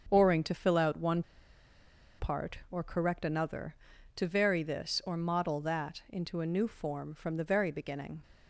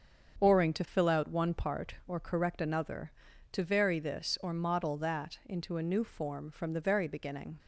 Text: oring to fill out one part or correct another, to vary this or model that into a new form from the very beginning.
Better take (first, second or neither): second